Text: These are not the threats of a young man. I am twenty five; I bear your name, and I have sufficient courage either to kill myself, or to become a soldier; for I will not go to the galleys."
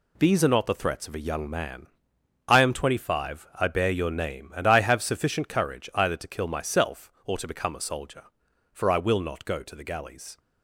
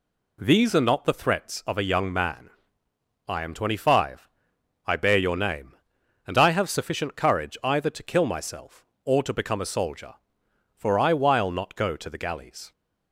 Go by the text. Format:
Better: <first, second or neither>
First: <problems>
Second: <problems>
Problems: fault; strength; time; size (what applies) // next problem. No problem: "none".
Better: first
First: none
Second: says "while" for "will"; at 11.1 s